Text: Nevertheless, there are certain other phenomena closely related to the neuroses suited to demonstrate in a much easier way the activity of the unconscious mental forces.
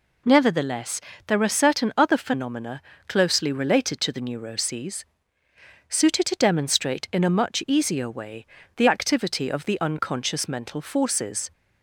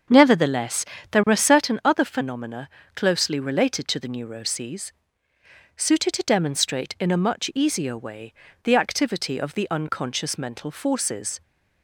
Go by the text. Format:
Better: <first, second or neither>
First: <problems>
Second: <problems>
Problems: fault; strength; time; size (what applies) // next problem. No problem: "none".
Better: first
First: pauses between "phenomena" and "closely"; slight; at 2.8 s; 0.28 s long // pauses between "neuroses" and "suited"; noticeable; at 5.0 s; 0.86 s long // pauses between "way" and "the"; slight; at 8.4 s; 0.30 s long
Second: starts louder than the rest; until 1.7 s; 7 dB // pauses between "phenomena" and "closely"; slight; at 2.6 s; 0.28 s long // pauses between "neuroses" and "suited"; noticeable; at 4.9 s; 0.86 s long // pauses between "way" and "the"; slight; at 8.3 s; 0.30 s long